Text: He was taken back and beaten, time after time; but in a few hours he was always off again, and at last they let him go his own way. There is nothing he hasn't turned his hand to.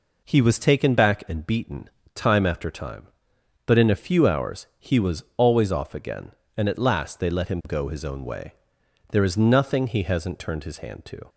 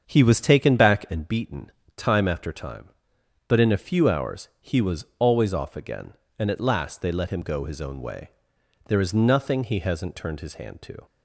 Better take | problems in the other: first | starts louder than the rest; until 1.3 s; 7 dB

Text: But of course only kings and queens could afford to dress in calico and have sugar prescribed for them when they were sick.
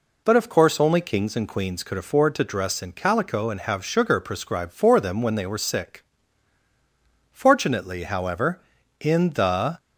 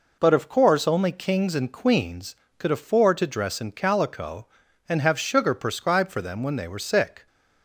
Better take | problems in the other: second | goes on to say "Fortunately however in the"; strong; from 7.3 s on; 2.4 s long

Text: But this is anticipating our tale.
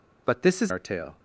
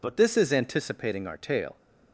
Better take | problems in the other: second | skips "anticipating"; at 0.7 s

